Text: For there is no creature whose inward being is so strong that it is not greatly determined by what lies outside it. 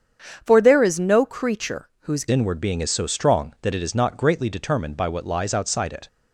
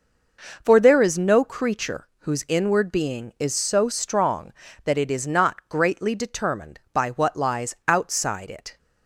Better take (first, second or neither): second